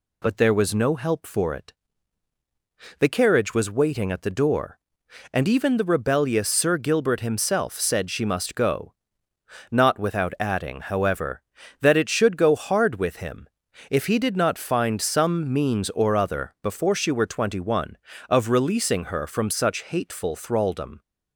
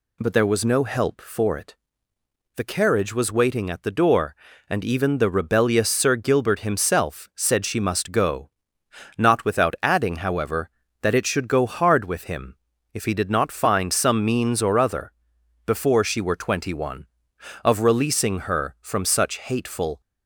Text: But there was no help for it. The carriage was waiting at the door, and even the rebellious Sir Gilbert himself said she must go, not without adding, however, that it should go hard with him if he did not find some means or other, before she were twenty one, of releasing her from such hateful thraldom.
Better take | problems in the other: first | pauses between "him" and "if"; slight; at 12.5 s; 0.36 s long; also in the first // stops before "thraldom"; at 20.0 s

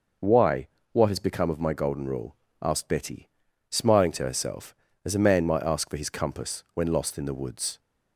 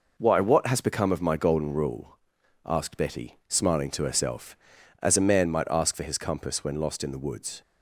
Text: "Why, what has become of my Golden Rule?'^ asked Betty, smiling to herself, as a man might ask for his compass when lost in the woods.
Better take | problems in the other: neither | none

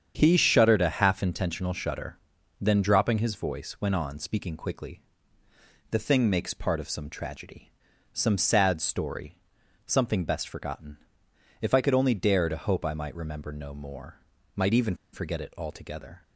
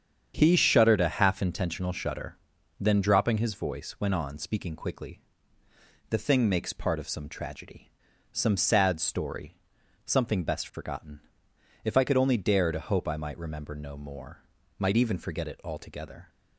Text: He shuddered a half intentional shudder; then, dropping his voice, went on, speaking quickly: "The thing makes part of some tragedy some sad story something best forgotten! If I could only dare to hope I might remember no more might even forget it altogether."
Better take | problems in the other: second | starts louder than the rest; strong; until 1.1 s; 8 dB; strong in the second // pauses between "tragedy" and "some"; at 7.6 s; 0.44 s long; also in the second // pauses between "story" and "something"; noticeable; at 9.3 s; 0.48 s long; noticeable in the second // pauses between "more" and "might"; slight; at 14.2 s; 0.34 s long; slight in the second // pauses between "even" and "forget"; slight; at 14.9 s; 0.18 s long

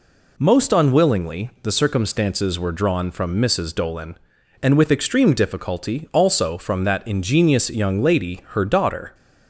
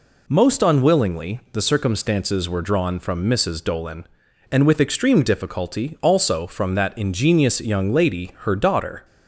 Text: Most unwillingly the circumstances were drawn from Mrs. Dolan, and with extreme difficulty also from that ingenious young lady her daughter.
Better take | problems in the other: neither | none

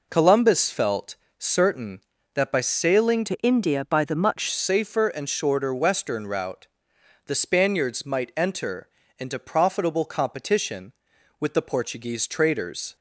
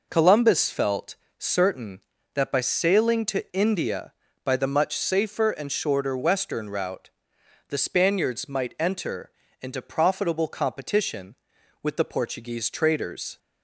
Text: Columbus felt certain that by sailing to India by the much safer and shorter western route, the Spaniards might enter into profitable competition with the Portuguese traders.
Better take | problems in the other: second | pauses between "felt" and "certain"; slight; at 1.1 s; 0.22 s long; slight in the second // changes voice from "to" to "much"; from 3.2 to 4.4 s; 1.2 s long // pauses between "enter" and "into"; slight; at 8.8 s; 0.32 s long; slight in the second

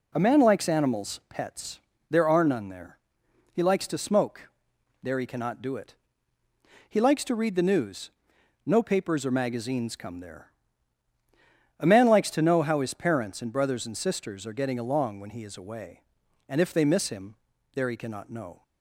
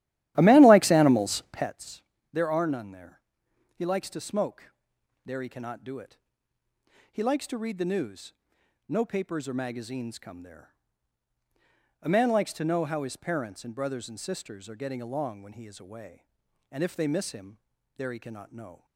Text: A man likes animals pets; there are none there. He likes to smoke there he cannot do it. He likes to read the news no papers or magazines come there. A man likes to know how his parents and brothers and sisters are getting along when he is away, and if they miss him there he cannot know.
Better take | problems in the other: first | starts louder than the rest; strong; until 1.8 s; 13.5 dB // pauses between "smoke" and "there"; noticeable; at 4.7 s; 0.54 s long; noticeable in the first // pauses between "news" and "no"; noticeable; at 8.3 s; 0.56 s long; noticeable in the first // pauses between "him" and "there"; at 17.5 s; 0.38 s long; also in the first

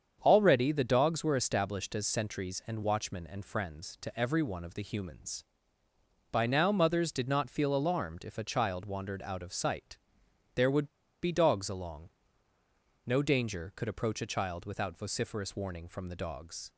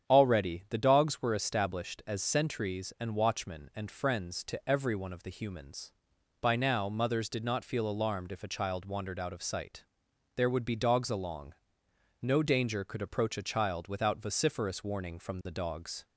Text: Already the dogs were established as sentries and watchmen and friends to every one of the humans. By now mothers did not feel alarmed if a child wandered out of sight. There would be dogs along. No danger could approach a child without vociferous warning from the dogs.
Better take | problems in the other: second | starts louder than the rest; strong; until 1.2 s; 7.5 dB; strong in the second // pauses between "would" and "be"; at 10.8 s; 0.37 s long

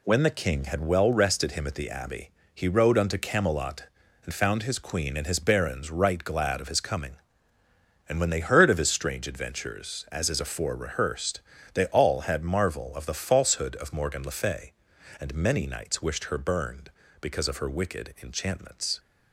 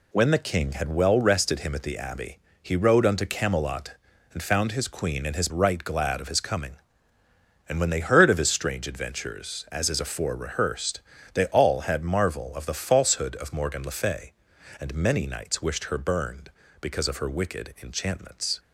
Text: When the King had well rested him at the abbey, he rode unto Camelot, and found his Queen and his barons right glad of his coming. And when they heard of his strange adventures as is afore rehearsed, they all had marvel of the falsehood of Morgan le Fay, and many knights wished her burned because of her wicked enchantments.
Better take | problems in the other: first | skips "barons"; at 5.4 s

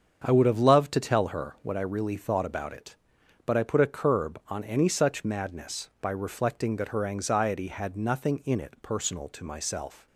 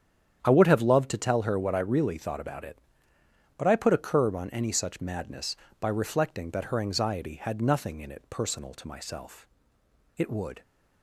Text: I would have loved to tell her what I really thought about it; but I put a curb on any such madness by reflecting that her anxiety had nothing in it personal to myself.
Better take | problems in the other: first | starts louder than the rest; strong; until 1.4 s; 9 dB; strong in the first // goes on to say "It would"; slight; from 10.1 s on; 0.46 s long

